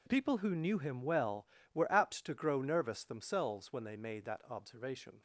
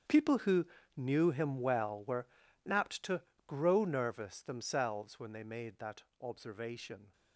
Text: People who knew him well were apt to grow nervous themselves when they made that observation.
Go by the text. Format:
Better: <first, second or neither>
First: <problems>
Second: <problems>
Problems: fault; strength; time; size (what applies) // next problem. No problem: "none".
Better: first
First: none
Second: gets quieter; strong; throughout; 16 dB // pauses between "who" and "knew"; slight; at 0.6 s; 0.30 s long // pauses between "were" and "apt"; at 2.2 s; 0.40 s long // pauses between "to" and "grow"; slight; at 3.2 s; 0.26 s long // pauses between "that" and "observation"; slight; at 6.0 s; 0.16 s long